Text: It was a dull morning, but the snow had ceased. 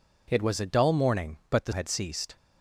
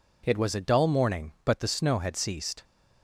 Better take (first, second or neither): second